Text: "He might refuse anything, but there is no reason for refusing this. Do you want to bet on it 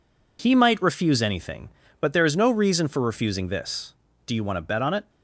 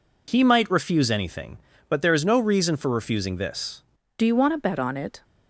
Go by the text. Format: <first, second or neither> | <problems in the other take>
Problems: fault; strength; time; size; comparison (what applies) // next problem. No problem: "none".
first | changes voice at "Do"; from 4.1 s on; 1.1 s long